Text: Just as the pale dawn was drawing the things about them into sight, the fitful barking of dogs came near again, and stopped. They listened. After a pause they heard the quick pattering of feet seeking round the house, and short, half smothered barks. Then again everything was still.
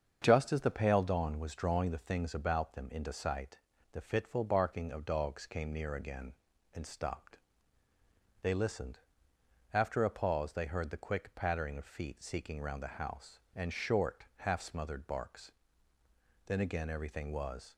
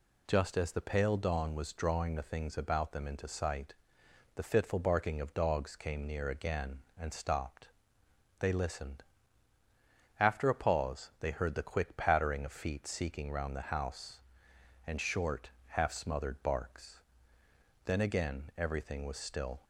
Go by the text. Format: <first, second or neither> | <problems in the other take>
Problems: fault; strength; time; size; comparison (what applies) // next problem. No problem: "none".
second | starts louder than the rest; until 1.2 s; 7 dB // stops before "still"; at 17.7 s